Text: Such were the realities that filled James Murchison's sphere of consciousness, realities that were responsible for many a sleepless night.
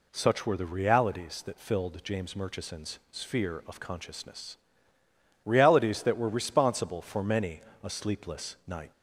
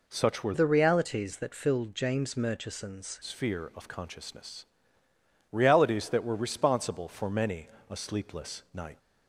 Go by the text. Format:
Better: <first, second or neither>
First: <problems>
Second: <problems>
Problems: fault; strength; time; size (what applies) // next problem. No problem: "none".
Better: first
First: pauses between "many" and "a"; slight; at 7.6 s; 0.22 s long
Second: changes voice from "the" to "Murchison's"; from 0.5 to 3.1 s; 2.6 s long // pauses between "many" and "a"; slight; at 7.6 s; 0.22 s long